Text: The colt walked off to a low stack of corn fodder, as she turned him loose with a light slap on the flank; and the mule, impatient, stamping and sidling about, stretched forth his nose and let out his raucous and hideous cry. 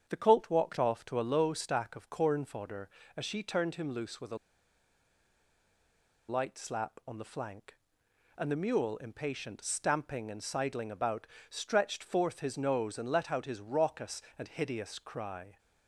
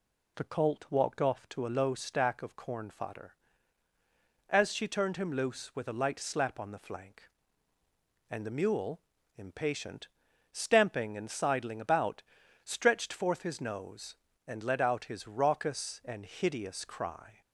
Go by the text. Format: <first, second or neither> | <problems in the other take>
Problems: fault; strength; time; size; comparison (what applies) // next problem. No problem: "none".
second | starts louder than the rest; strong; until 1.1 s; 8 dB // pauses between "a" and "light"; strong; at 4.3 s; 1.9 s long